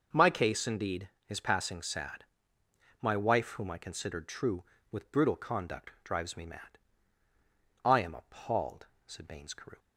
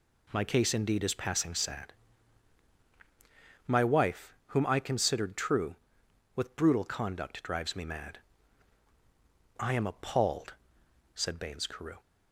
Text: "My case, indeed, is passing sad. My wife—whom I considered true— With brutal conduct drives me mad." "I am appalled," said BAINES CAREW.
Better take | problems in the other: neither | none

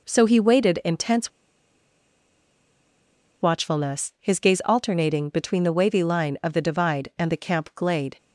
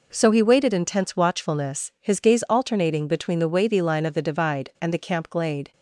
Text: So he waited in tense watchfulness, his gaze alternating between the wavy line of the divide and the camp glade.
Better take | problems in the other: second | pauses between "tense" and "watchfulness"; strong; at 1.3 s; 2.1 s long

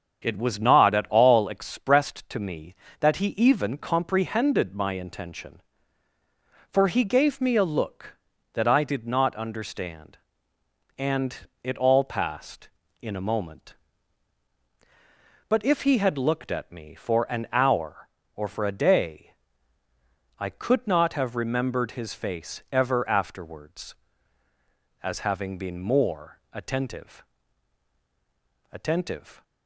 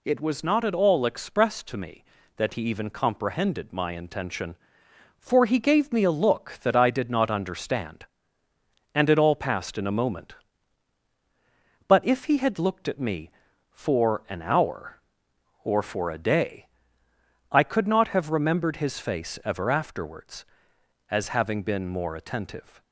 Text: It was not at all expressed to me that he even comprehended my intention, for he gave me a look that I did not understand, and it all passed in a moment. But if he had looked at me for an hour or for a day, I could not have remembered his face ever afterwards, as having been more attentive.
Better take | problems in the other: second | starts louder than the rest; strong; until 1.2 s; 7.5 dB // pauses between "and" and "it"; slight; at 11.3 s; 0.30 s long // says "attentive" twice; at 28.7 s

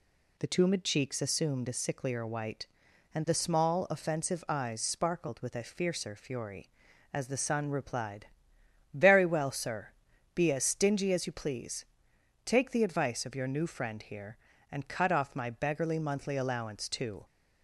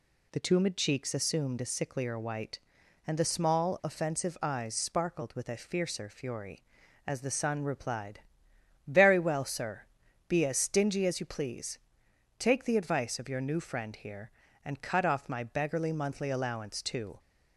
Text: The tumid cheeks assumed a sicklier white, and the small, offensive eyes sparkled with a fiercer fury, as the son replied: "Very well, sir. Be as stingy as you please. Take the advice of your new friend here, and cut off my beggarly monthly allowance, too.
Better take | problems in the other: neither | none

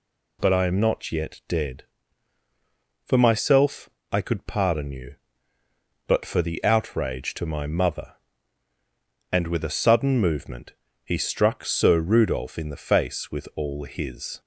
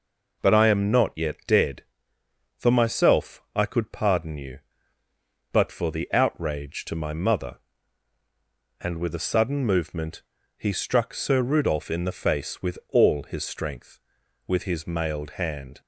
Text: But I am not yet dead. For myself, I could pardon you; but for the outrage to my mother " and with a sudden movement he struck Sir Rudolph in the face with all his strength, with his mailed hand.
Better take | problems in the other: second | pauses between "movement" and "he"; slight; at 10.7 s; 0.32 s long; slight in the second // stops before "strength with his mailed hand"; at 14.3 s

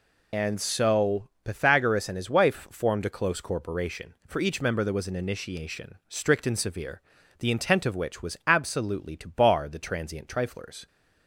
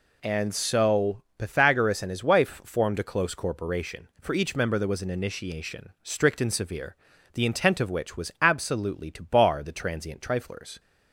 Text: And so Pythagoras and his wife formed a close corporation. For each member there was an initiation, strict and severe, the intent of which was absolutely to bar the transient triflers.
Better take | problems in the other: second | loses the start of "And"; at 0.3 s; 45 ms // pauses between "so" and "Pythagoras"; slight; at 1.2 s; 0.16 s long; slight in the second

